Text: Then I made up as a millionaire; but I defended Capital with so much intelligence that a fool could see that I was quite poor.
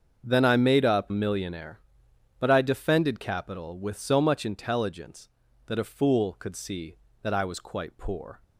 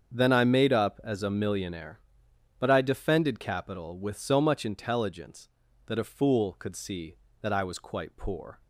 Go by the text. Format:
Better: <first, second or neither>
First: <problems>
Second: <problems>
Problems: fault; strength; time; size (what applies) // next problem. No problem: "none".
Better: second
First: starts louder than the rest; until 1.2 s; 7 dB // skips "as a"; at 1.1 s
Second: starts louder than the rest; strong; until 1.1 s; 7 dB